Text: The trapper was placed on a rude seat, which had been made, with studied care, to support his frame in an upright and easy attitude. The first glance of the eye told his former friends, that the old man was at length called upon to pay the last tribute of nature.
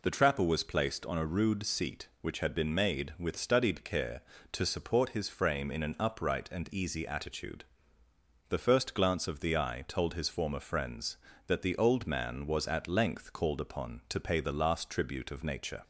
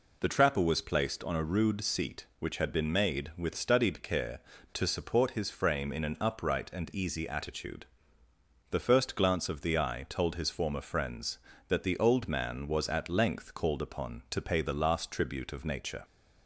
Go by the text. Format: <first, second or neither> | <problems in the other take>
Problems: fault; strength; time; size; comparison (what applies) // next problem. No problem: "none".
neither | none